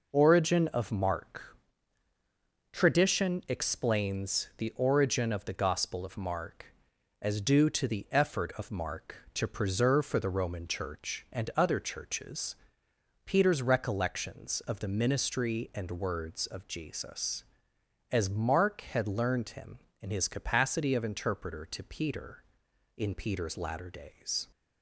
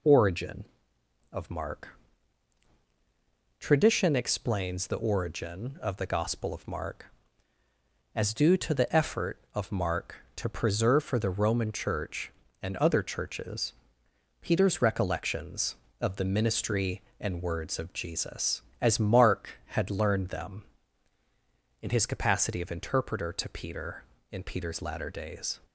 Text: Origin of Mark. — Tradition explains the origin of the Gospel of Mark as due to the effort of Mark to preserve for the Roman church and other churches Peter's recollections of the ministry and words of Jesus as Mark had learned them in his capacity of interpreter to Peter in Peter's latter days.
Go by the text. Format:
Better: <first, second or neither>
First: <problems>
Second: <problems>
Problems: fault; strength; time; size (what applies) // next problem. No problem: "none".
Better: second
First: pauses between "churches" and "Peter's"; noticeable; at 12.5 s; 0.72 s long // says "him" for "them"; at 19.5 s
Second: pauses between "churches" and "Peter's"; noticeable; at 13.7 s; 0.66 s long